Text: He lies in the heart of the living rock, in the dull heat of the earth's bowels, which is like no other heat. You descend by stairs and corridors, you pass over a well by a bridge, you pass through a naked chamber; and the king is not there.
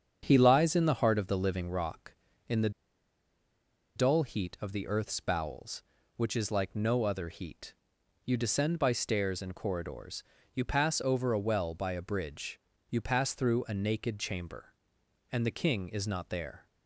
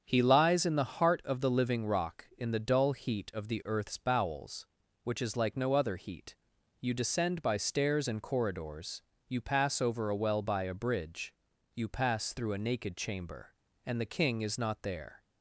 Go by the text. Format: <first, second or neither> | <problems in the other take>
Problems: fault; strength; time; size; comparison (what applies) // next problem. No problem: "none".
second | starts louder than the rest; strong; until 1.2 s; 7.5 dB; strong in the second // pauses between "the" and "dull"; strong; at 2.6 s; 1.2 s long